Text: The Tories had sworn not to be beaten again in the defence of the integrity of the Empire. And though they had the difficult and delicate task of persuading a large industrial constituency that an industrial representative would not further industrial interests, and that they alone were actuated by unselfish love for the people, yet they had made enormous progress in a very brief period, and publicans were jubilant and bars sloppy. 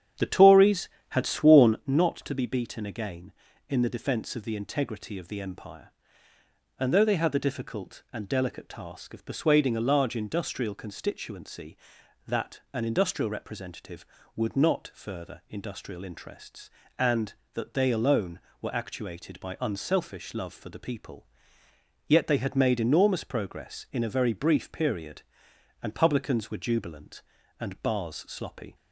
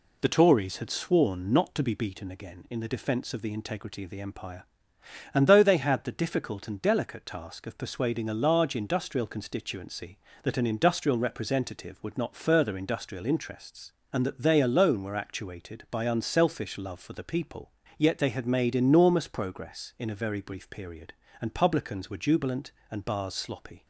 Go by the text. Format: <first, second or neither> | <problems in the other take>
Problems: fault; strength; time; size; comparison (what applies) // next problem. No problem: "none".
second | starts louder than the rest; strong; until 1.9 s; 9 dB